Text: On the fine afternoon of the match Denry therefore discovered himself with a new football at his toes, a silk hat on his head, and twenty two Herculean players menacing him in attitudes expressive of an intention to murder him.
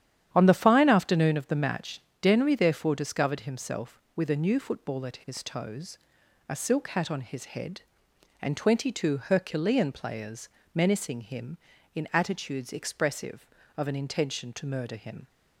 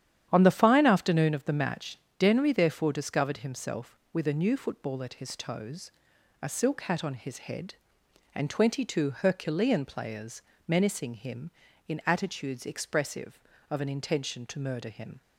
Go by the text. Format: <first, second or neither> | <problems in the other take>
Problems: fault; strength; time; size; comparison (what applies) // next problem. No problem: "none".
neither | starts louder than the rest; strong; the same in both // pauses between "match" and "Denry"; slight; the same in both // pauses between "players" and "menacing"; slight; the same in both